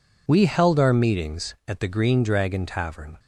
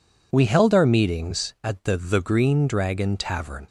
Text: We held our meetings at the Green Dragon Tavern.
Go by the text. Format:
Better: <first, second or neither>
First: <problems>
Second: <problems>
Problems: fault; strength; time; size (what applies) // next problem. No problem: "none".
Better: first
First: none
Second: says "the" twice; at 1.9 s